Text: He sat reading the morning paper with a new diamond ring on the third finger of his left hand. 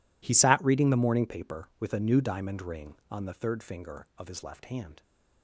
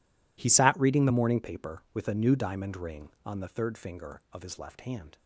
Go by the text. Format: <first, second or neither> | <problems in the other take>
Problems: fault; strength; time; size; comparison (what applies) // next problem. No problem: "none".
neither | none